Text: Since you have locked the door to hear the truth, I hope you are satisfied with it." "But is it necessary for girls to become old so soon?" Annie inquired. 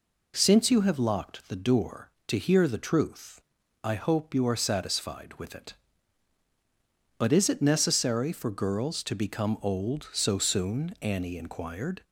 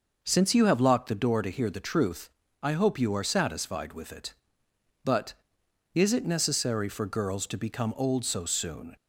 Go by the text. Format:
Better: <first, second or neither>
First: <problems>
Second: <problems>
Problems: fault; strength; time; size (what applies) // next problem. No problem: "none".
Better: first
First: none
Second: stops before "Annie inquired"; at 8.9 s